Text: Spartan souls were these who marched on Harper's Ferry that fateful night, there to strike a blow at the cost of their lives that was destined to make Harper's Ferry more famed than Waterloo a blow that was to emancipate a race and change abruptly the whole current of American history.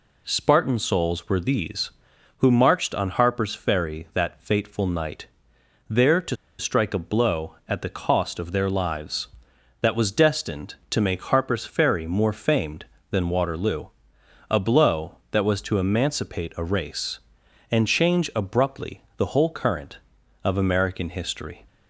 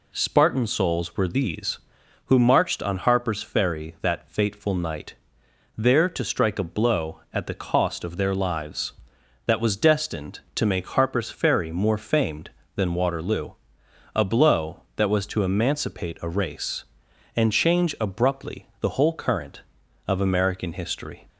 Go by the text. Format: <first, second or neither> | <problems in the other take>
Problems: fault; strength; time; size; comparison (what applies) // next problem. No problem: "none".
second | pauses between "to" and "strike"; slight; at 6.3 s; 0.23 s long // pauses between "Waterloo" and "a"; noticeable; at 13.8 s; 0.60 s long; noticeable in the second // pauses between "abruptly" and "the"; slight; at 19.0 s; 0.16 s long